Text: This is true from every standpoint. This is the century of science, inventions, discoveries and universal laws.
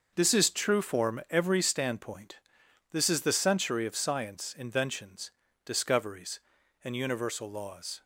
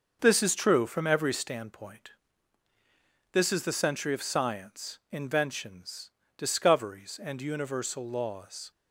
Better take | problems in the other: second | starts louder than the rest; noticeable; until 1.1 s; 6 dB; also in the second // says "form" for "from"; at 0.8 s

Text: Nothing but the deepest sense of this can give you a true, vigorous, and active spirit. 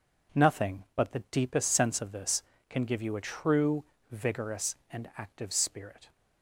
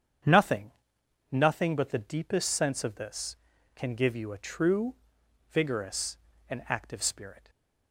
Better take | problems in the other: first | starts louder than the rest; strong; until 1.8 s; 8 dB // says "Nothing" twice; at 1.3 s // stays silent after the last word; slight; from 7.3 s on; 0.6 s long

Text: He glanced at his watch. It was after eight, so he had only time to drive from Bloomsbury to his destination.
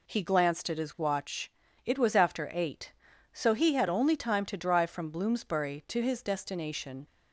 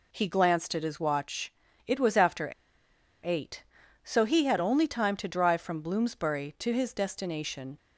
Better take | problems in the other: first | pauses between "after" and "eight"; noticeable; at 2.5 s; 0.72 s long

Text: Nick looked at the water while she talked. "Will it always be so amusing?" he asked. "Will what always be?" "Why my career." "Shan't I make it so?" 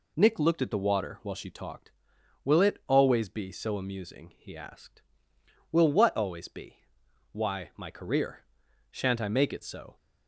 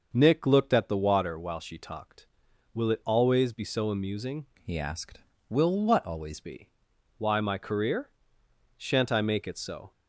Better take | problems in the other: first | starts louder than the rest; noticeable; until 1.1 s; 6 dB // changes voice from "he" to "always"; from 4.6 to 6.4 s; 1.8 s long

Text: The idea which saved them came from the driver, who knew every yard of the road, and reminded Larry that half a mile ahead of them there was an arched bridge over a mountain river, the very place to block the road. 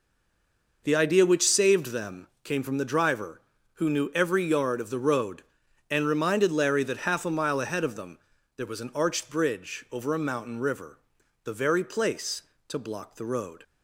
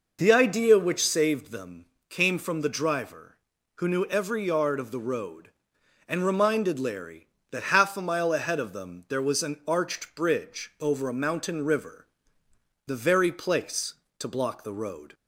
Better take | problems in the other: second | stays silent before the first word; slight; until 0.8 s; 0.8 s long // pauses between "them" and "came"; slight; at 2.2 s; 0.16 s long; slight in the second // pauses between "them" and "there"; at 8.1 s; 0.38 s long

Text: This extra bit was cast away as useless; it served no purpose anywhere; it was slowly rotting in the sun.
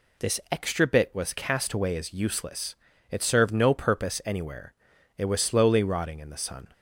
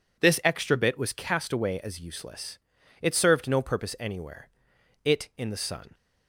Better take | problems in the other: first | skips "was slowly rotting"; at 5.3 s

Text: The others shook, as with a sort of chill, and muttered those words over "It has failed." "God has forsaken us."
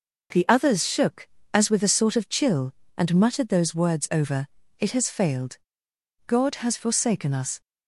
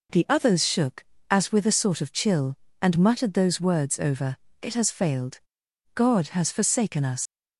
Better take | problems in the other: first | pauses between "over" and "It"; slight; at 4.3 s; 0.22 s long; slight in the first // leaves "us" unfinished; at 7.2 s; 85 ms

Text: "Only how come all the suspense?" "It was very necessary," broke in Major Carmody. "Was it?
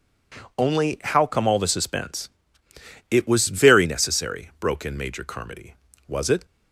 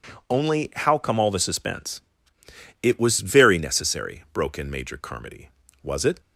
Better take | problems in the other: neither | none

